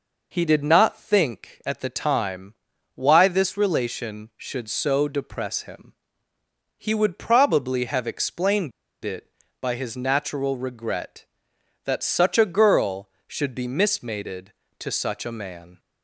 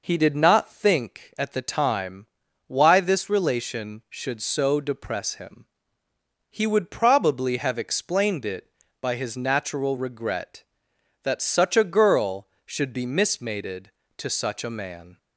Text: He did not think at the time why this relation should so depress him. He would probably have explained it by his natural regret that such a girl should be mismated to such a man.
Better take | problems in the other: second | pauses between "time" and "why"; at 2.5 s; 0.40 s long; also in the second // pauses between "explained" and "it"; slight; at 8.7 s; 0.31 s long

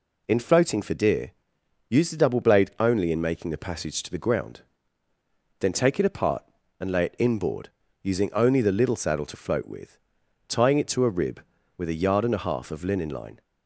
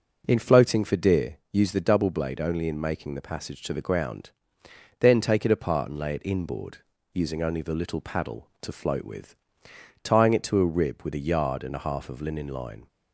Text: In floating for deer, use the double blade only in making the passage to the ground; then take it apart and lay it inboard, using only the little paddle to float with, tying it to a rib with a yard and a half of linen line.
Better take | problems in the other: second | says "saddle" for "paddle"; at 8.9 s

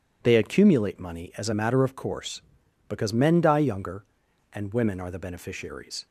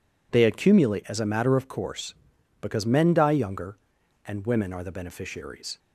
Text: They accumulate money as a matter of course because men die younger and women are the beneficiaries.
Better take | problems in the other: first | skips "money"; at 1.0 s

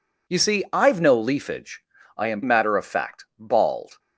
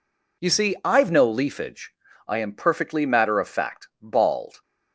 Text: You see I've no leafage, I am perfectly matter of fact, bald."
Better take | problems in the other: second | skips "perfectly"; at 2.4 s

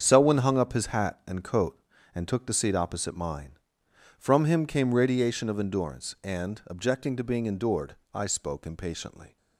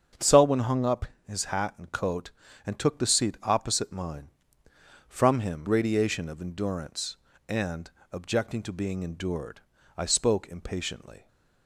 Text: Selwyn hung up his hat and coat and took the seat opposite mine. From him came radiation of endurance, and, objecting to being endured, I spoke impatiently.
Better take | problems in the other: first | starts louder than the rest; strong; until 1.4 s; 7.5 dB; strong in the first // pauses between "up" and "his"; slight; at 1.0 s; 0.22 s long // skips "came"; at 5.6 s

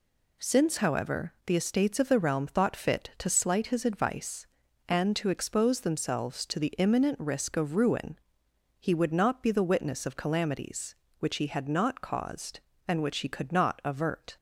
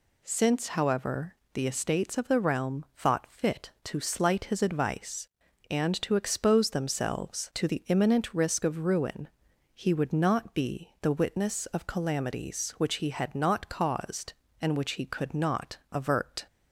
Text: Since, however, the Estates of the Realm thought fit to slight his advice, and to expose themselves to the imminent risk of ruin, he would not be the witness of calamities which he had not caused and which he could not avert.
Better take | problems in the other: neither | none

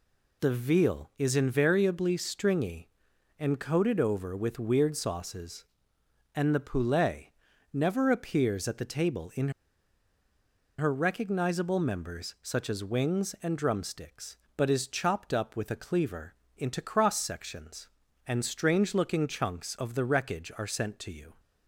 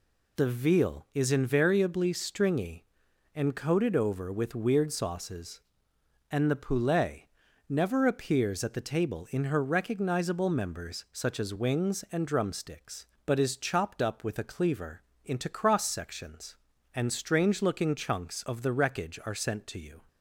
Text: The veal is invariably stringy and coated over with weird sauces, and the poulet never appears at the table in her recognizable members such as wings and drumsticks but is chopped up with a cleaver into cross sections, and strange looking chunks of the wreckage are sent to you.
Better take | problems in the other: second | pauses between "poulet" and "never"; at 7.2 s; 0.44 s long; also in the second // pauses between "in" and "her"; strong; at 9.4 s; 1.2 s long // pauses between "cleaver" and "into"; slight; at 16.3 s; 0.24 s long; slight in the second

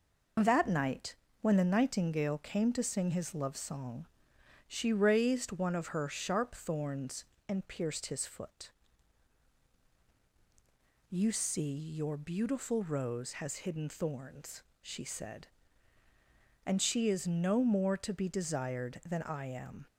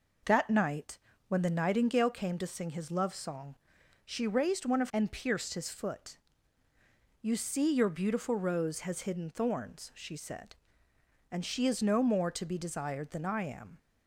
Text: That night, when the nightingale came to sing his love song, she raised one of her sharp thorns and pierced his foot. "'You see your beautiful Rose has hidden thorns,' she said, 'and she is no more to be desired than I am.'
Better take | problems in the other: first | skips "her sharp thorns"; at 4.9 s

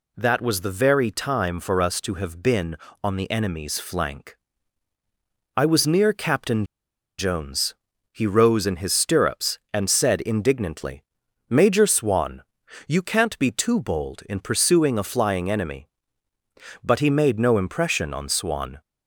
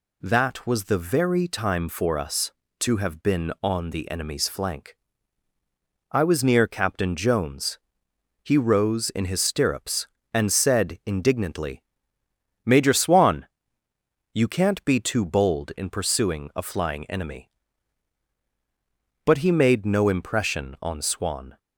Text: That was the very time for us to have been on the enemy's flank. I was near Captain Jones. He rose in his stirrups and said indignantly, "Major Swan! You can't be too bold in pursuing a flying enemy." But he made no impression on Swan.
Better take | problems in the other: second | pauses between "Captain" and "Jones"; noticeable; at 6.6 s; 0.54 s long

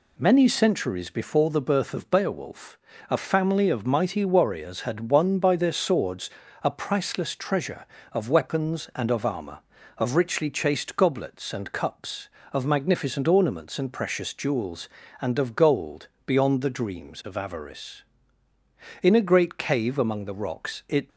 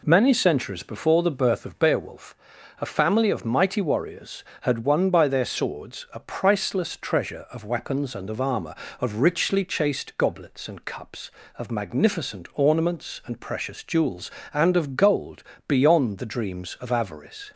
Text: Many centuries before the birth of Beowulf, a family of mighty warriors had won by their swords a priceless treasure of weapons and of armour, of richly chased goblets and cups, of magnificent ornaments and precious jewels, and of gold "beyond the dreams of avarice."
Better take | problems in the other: second | pauses between "swords" and "a"; slight; at 6.2 s; 0.34 s long // pauses between "gold" and "beyond"; slight; at 16.0 s; 0.16 s long; slight in the second // goes on to say "In a great cave among the rocks it"; strong; from 19.0 s on; 2.0 s long

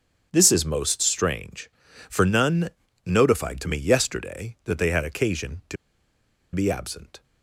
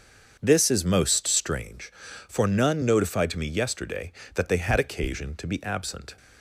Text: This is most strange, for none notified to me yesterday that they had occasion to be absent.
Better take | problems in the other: second | starts louder than the rest; strong; until 1.3 s; 7.5 dB; also in the second // pauses between "none" and "notified"; slight; at 2.6 s; 0.36 s long // pauses between "to" and "be"; noticeable; at 5.7 s; 0.78 s long

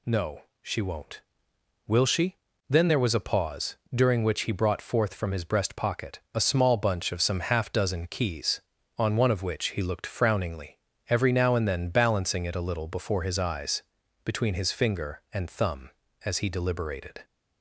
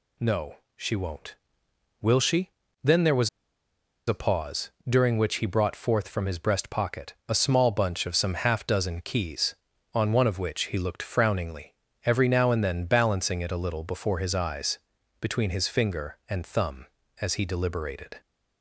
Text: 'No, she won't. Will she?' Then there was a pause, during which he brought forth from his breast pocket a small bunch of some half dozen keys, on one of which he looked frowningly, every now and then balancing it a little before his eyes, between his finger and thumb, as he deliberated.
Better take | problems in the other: first | pauses between "was" and "a"; noticeable; at 3.2 s; 0.79 s long

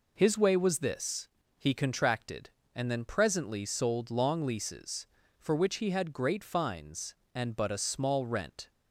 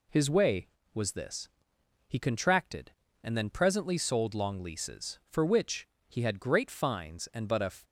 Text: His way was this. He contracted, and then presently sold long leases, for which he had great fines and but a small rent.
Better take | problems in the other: first | pauses between "which" and "he"; slight; at 5.8 s; 0.22 s long // stops before "small rent"; at 7.8 s

